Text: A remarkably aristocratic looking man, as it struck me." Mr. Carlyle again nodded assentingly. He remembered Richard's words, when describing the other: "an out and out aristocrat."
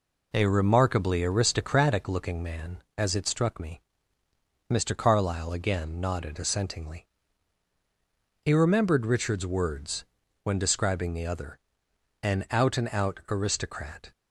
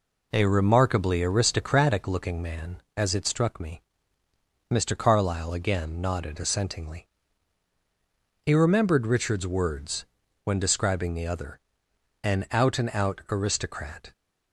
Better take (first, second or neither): neither